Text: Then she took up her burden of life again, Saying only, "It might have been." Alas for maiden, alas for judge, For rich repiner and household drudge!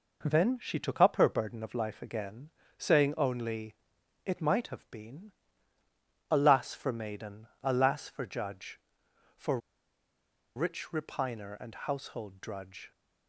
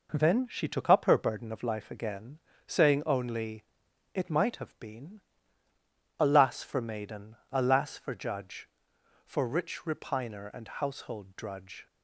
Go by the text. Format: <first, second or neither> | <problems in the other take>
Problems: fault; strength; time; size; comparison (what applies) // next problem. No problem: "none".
second | pauses between "For" and "rich"; at 9.5 s; 0.98 s long